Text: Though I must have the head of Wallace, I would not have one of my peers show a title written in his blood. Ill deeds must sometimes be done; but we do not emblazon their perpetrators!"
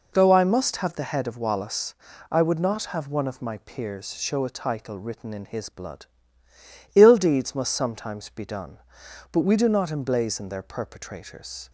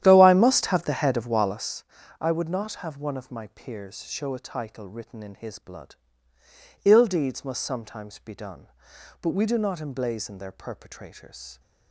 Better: first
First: none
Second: starts louder than the rest; strong; until 1.7 s; 11 dB

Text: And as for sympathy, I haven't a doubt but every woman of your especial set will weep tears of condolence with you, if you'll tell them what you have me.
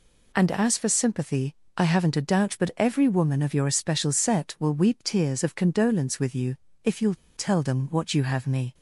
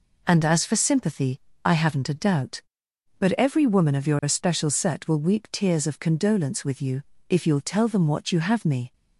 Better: second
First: pauses between "you'll" and "tell"; slight; at 7.1 s; 0.20 s long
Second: none

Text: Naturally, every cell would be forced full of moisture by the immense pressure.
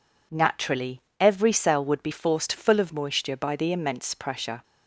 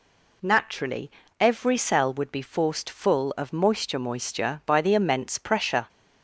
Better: first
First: none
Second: says "moisture" twice; at 3.9 s

